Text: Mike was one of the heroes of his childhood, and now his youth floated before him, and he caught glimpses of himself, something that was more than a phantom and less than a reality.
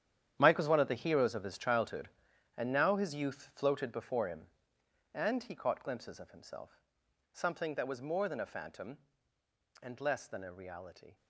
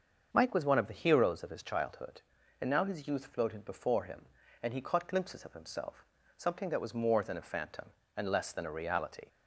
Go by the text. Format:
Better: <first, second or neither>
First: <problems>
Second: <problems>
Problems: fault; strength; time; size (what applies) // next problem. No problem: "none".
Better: second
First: gets quieter; strong; throughout; 13.5 dB // starts louder than the rest; strong; until 1.4 s; 10 dB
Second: starts louder than the rest; until 1.3 s; 6.5 dB